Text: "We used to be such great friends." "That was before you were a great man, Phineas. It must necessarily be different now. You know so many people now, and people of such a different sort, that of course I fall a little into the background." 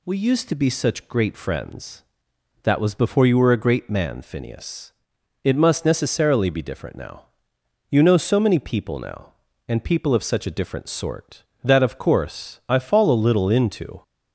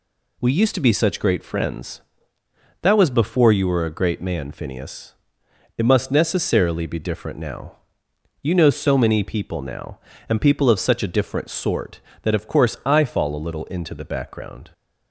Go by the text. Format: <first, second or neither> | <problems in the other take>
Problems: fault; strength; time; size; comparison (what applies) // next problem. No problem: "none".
second | stops before "the background"; at 14.0 s